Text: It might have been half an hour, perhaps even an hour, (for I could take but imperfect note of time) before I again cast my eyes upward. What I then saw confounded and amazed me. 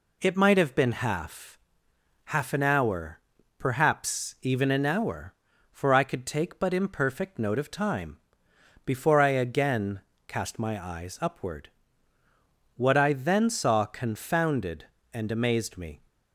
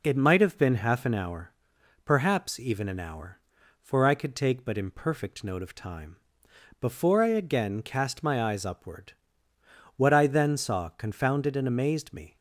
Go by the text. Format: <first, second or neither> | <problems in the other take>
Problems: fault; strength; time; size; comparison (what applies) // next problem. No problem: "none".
second | says "half" twice; at 2.2 s // pauses between "again" and "cast"; slight; at 10.0 s; 0.26 s long